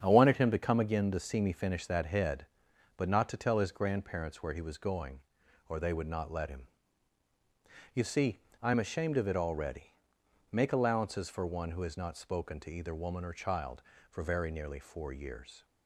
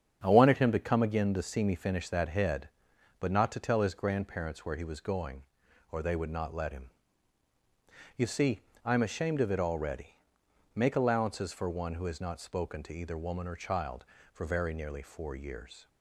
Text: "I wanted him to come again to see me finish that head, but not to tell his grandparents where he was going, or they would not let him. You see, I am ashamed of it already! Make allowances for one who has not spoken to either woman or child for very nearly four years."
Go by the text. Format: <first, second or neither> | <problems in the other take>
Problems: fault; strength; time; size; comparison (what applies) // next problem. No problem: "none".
neither | starts louder than the rest; strong; the same in both